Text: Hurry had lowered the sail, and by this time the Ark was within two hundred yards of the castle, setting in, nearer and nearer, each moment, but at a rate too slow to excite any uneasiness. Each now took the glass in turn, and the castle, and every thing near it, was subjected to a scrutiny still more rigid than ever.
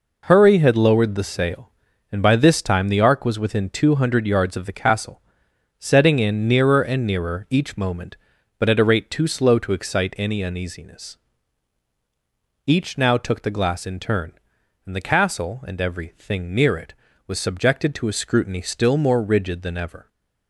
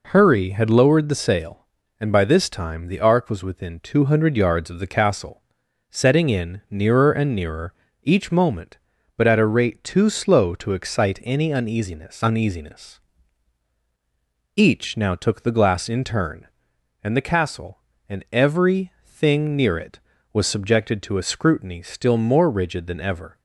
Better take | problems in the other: first | says "uneasiness" twice; at 12.2 s

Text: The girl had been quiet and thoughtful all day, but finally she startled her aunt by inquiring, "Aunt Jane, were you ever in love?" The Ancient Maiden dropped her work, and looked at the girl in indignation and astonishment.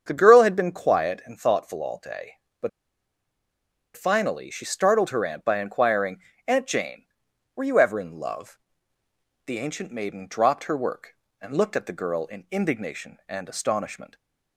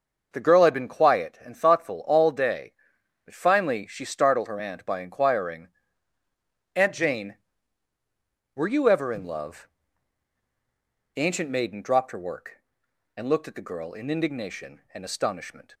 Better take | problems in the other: second | starts louder than the rest; strong; until 1.0 s; 7.5 dB; also in the second // pauses between "but" and "finally"; strong; at 2.6 s; 1.2 s long

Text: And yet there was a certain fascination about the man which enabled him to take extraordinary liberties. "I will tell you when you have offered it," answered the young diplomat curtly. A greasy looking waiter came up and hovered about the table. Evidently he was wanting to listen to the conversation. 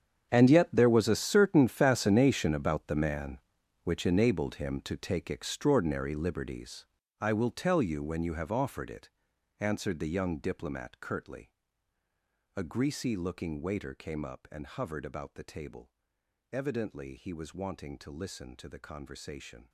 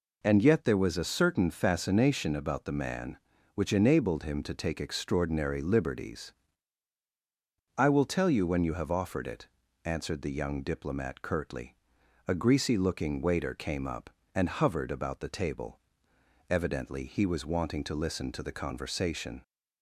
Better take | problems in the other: second | gets quieter; strong; throughout; 17 dB

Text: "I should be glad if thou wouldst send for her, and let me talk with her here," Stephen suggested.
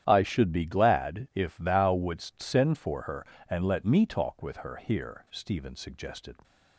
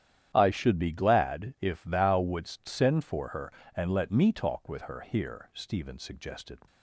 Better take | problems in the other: neither | starts louder than the rest; strong; the same in both

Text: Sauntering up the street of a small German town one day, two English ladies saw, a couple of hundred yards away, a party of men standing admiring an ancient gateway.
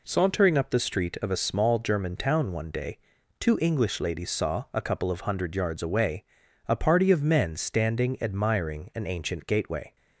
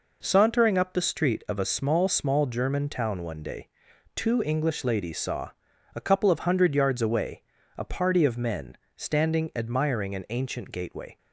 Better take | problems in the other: first | says "small" twice; at 2.0 s // pauses between "men" and "standing"; slight; at 8.7 s; 0.18 s long

